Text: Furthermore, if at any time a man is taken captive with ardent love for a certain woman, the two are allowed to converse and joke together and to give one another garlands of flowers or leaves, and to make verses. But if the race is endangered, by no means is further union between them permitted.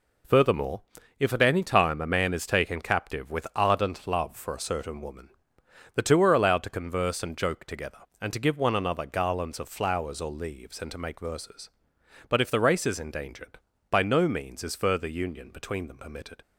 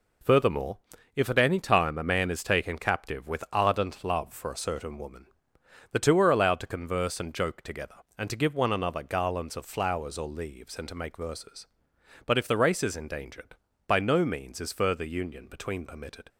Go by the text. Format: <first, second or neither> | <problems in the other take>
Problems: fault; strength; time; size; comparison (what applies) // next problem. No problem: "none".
first | skips "them"; at 15.8 s